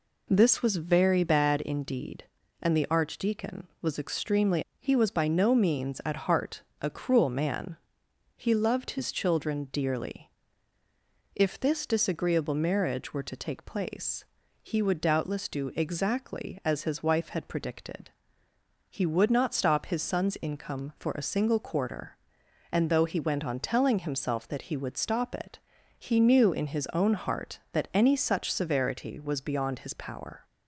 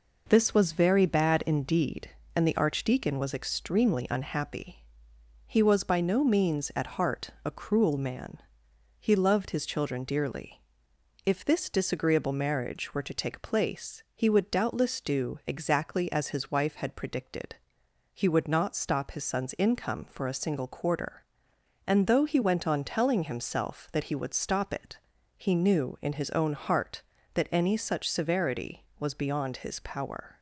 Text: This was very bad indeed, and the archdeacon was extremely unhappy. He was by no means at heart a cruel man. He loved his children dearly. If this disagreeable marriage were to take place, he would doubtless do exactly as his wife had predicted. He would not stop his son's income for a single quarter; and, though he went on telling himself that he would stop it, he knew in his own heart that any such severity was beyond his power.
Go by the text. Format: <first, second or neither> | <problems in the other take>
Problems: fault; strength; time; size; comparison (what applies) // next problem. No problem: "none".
second | skips "unhappy"; at 4.6 s // pauses between "heart" and "a"; slight; at 6.6 s; 0.18 s long; slight in the second